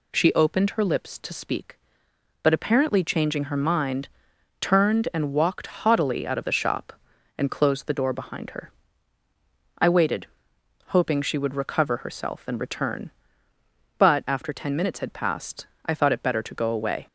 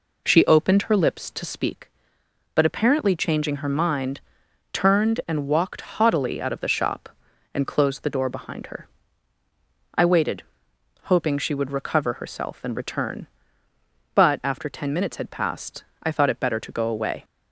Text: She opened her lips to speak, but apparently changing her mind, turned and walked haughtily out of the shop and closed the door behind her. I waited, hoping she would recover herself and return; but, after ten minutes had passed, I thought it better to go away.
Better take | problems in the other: first | starts louder than the rest; until 1.8 s; 3.5 dB

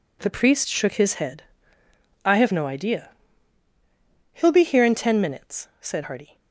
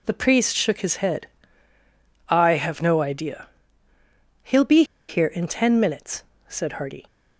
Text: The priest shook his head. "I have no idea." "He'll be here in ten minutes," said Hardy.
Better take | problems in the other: first | pauses between "be" and "here"; slight; at 4.8 s; 0.25 s long

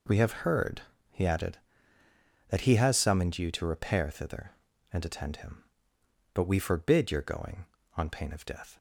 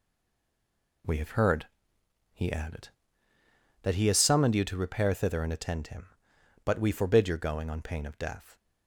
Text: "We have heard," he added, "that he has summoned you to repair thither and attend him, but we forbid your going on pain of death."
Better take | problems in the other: first | stays silent before the first word; until 1.0 s; 1.0 s long

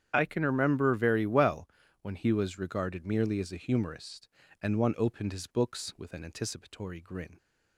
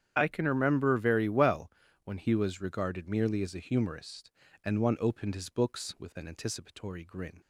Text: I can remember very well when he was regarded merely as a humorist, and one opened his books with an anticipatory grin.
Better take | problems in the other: neither | starts louder than the rest; strong; the same in both // pauses between "well" and "when"; slight; the same in both

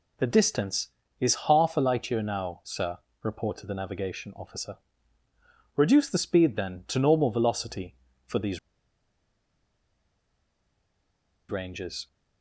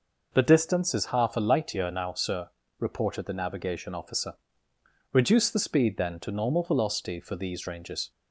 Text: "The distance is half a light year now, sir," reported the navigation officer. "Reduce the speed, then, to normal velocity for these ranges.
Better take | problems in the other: second | pauses between "these" and "ranges"; strong; at 8.5 s; 2.9 s long

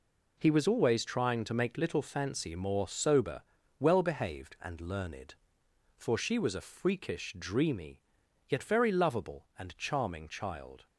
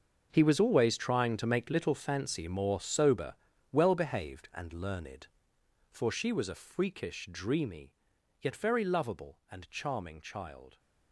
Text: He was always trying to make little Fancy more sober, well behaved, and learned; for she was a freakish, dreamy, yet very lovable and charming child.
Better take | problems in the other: first | gets quieter; strong; throughout; 14.5 dB

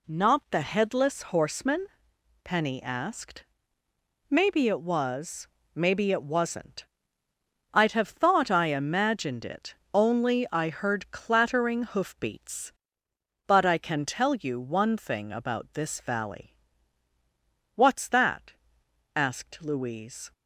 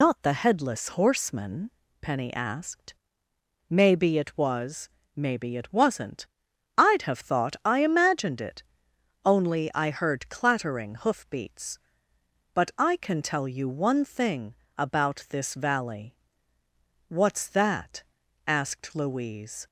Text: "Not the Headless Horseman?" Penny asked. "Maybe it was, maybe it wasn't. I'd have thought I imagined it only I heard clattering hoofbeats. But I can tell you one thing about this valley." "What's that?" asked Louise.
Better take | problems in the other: first | loses the start of "Not"; at 0.0 s; 90 ms // pauses between "it" and "only"; noticeable; at 8.6 s; 0.60 s long; slight in the first // pauses between "thing" and "about"; slight; at 14.5 s; 0.24 s long

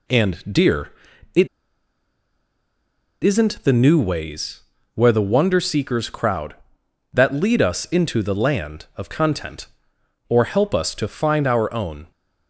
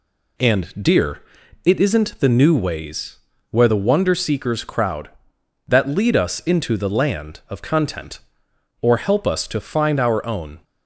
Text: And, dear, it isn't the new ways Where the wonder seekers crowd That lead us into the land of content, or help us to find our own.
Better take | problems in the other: second | pauses between "it" and "isn't"; strong; at 1.4 s; 1.7 s long // pauses between "ways" and "Where"; slight; at 4.6 s; 0.34 s long; slight in the second

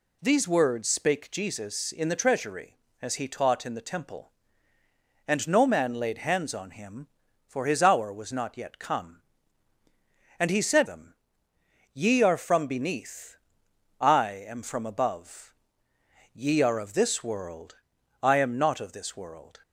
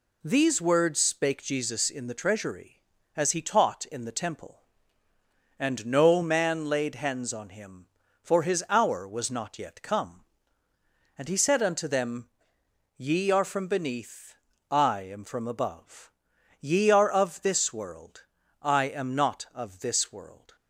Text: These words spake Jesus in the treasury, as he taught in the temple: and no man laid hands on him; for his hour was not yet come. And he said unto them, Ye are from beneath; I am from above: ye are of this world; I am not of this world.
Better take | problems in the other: second | skips "unto"; at 10.8 s

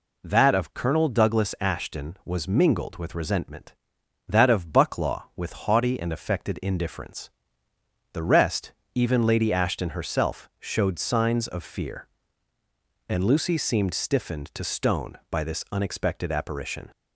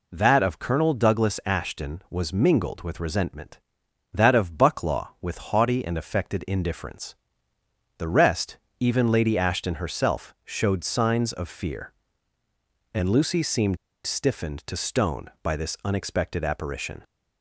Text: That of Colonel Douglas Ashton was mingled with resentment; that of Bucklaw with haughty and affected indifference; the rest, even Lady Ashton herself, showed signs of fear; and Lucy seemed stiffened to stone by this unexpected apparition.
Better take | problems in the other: first | pauses between "seemed" and "stiffened"; slight; at 13.7 s; 0.30 s long

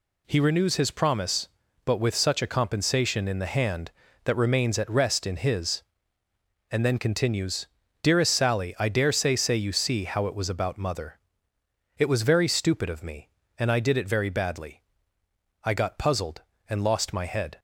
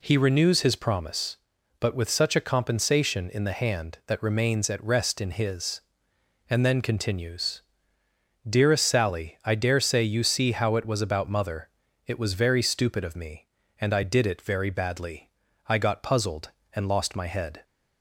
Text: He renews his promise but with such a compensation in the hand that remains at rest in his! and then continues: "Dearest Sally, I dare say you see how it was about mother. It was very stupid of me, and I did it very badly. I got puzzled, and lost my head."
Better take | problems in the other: second | says "say" twice; at 9.3 s

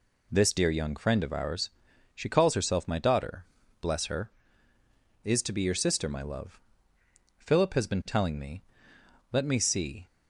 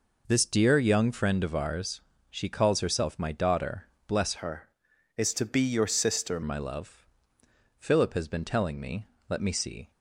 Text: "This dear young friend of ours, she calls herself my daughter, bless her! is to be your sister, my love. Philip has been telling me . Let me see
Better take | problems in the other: first | changes voice from "her" to "sister"; from 4.3 to 6.4 s; 2.1 s long

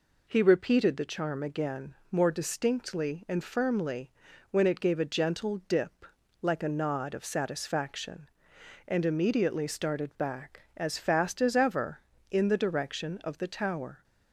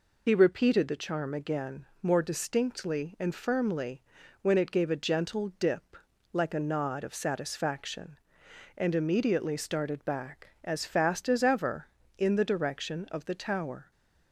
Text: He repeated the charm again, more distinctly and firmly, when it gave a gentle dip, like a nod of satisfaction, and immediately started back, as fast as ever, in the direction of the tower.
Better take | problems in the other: first | loses the start of "He"; at 0.2 s; 55 ms

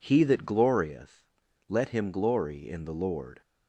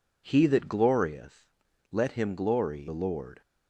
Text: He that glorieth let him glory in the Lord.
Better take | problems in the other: first | pauses between "glorieth" and "let"; noticeable; at 1.4 s; 0.46 s long; noticeable in the first // skips "in"; at 2.8 s

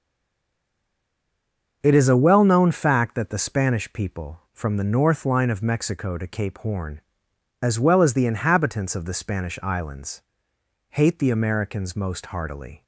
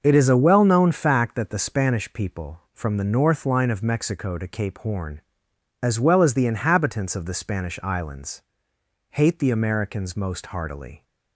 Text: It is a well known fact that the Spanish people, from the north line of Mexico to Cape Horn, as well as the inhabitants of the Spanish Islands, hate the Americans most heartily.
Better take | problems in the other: second | stays silent before the first word; noticeable; until 1.8 s; 1.8 s long // starts louder than the rest; noticeable; until 2.8 s; 6 dB; noticeable in the second

